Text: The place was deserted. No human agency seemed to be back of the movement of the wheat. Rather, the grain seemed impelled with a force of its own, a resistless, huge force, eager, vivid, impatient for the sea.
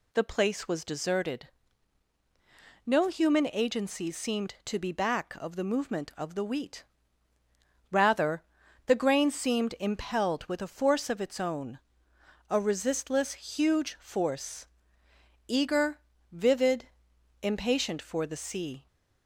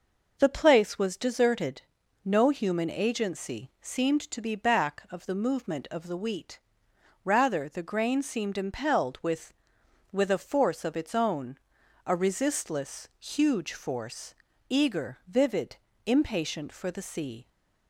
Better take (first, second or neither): first